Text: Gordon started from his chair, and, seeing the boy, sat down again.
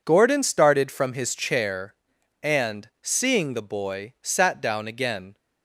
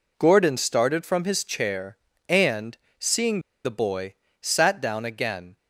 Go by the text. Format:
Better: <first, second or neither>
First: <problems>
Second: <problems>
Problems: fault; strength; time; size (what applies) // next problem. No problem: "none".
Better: first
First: none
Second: pauses between "seeing" and "the"; slight; at 3.4 s; 0.23 s long